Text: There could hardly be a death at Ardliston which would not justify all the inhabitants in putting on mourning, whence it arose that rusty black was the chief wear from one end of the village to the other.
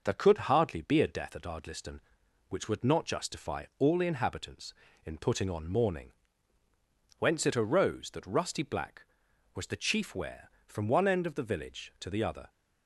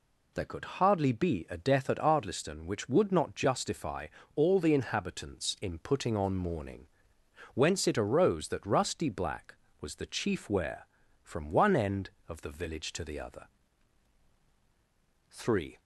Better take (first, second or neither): first